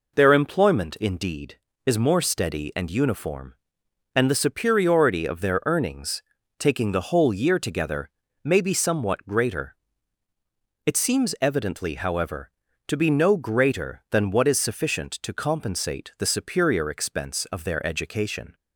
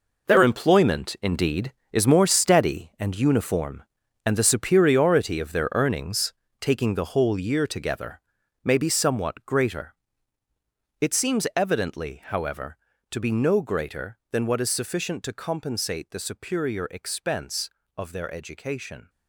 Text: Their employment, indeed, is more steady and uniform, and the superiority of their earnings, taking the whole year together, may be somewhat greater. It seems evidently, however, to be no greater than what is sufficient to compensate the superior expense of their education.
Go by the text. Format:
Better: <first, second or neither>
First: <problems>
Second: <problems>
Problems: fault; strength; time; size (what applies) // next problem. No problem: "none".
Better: first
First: none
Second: gets quieter; strong; throughout; 11 dB